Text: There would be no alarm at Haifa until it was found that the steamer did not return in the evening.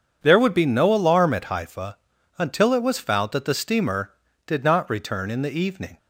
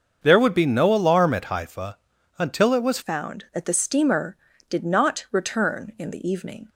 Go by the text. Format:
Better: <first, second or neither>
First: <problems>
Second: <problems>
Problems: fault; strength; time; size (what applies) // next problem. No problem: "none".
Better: first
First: starts louder than the rest; strong; until 1.2 s; 7.5 dB // pauses between "Haifa" and "until"; at 1.9 s; 0.40 s long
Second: starts louder than the rest; until 1.2 s; 6.5 dB // pauses between "Haifa" and "until"; at 1.9 s; 0.40 s long // changes voice at "found"; from 3.0 s on; 3.6 s long